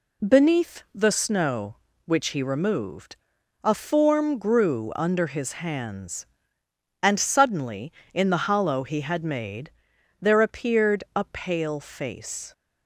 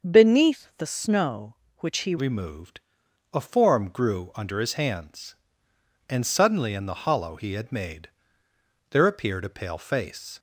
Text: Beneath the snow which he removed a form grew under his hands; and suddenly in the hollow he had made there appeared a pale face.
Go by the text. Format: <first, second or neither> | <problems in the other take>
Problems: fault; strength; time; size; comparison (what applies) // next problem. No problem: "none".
first | starts louder than the rest; until 1.1 s; 6 dB // changes voice at "removed"; from 2.1 s on; 8.2 s long // pauses between "removed" and "a"; noticeable; at 2.8 s; 0.50 s long; noticeable in the first // pauses between "made" and "there"; noticeable; at 8.0 s; 0.80 s long; noticeable in the first